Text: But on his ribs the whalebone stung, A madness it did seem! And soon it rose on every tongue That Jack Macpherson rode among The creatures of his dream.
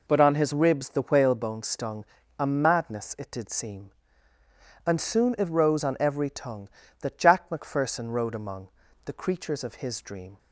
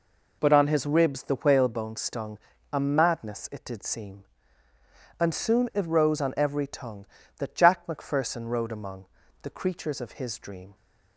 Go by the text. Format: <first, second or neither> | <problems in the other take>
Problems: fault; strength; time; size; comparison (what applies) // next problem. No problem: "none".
neither | pauses between "among" and "The"; the same in both